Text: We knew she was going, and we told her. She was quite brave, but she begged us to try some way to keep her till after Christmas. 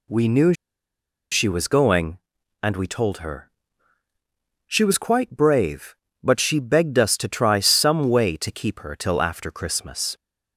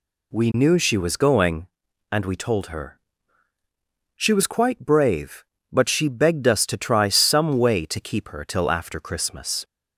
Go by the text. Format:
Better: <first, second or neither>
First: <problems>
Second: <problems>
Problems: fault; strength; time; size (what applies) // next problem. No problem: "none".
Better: second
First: pauses between "knew" and "she"; noticeable; at 0.5 s; 0.76 s long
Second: none